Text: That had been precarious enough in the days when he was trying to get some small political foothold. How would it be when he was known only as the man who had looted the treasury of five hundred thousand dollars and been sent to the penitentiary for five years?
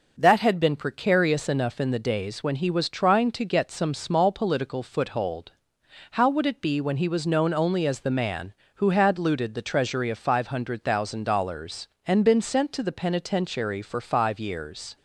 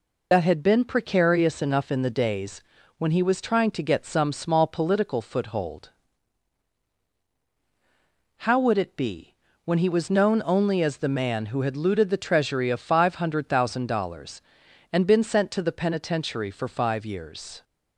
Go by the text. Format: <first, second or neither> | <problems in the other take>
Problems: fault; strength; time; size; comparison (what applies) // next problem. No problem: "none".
first | loses the start of "That"; at 0.3 s; 60 ms // pauses between "days" and "when"; slight; at 2.6 s; 0.36 s long // pauses between "be" and "when"; slight; at 9.3 s; 0.32 s long